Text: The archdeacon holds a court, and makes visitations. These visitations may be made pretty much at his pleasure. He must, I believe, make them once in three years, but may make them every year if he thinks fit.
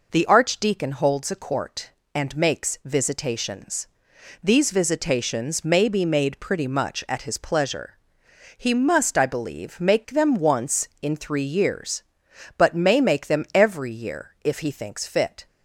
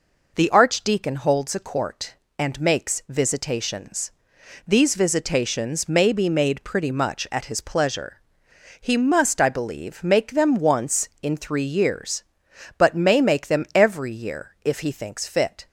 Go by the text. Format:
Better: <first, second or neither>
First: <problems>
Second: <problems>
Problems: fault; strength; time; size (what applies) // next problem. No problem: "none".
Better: neither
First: none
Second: none